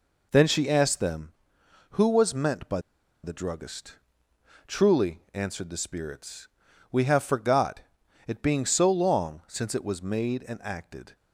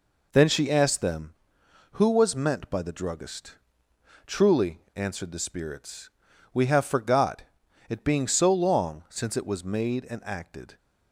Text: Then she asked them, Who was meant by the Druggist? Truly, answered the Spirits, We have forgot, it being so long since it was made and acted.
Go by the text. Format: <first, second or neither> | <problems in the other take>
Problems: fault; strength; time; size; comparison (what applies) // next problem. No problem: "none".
second | pauses between "by" and "the"; at 2.8 s; 0.42 s long